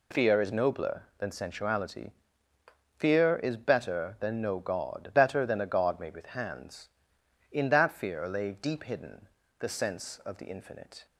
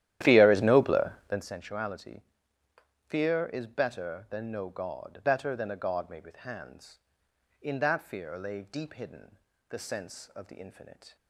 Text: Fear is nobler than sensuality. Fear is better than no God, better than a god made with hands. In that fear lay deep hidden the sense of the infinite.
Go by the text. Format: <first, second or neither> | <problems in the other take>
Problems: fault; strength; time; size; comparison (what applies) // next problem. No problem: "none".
first | starts louder than the rest; strong; until 1.6 s; 12 dB // pauses between "hidden" and "the"; slight; at 9.3 s; 0.32 s long; slight in the first